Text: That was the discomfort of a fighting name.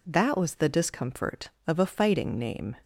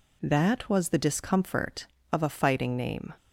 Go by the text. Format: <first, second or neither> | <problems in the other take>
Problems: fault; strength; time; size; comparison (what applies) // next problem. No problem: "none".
neither | none